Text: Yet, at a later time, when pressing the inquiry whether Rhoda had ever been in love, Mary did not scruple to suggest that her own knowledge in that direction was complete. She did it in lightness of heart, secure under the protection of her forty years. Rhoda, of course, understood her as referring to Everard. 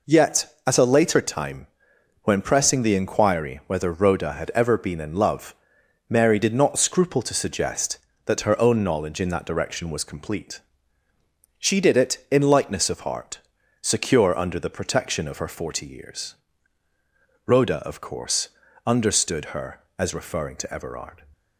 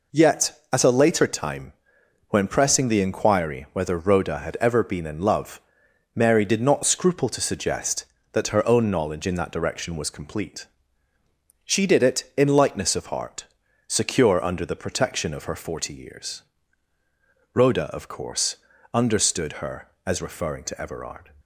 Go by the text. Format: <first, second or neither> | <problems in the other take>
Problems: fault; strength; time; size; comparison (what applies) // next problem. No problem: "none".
neither | none